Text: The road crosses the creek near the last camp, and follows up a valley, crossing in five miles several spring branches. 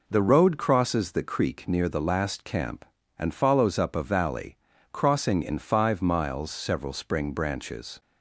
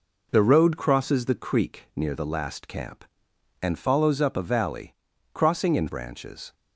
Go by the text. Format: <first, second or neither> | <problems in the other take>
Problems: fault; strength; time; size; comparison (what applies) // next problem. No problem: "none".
first | skips "five miles several spring"; at 5.8 s